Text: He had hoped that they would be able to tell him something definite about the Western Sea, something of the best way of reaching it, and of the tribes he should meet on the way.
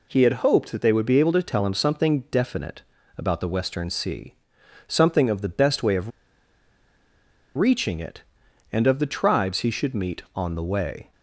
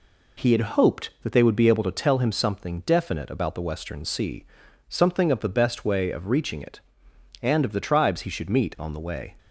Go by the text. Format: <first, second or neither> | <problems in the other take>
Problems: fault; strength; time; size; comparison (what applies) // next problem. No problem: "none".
second | pauses between "definite" and "about"; slight; at 2.8 s; 0.36 s long // pauses between "of" and "reaching"; strong; at 6.1 s; 1.4 s long